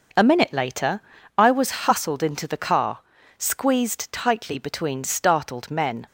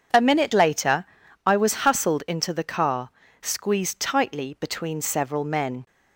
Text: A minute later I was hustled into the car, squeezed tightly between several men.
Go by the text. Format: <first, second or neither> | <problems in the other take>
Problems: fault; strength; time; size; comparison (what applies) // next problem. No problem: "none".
second | pauses between "later" and "I"; at 0.9 s; 0.38 s long; also in the second // says "startled" for "several"; at 5.0 s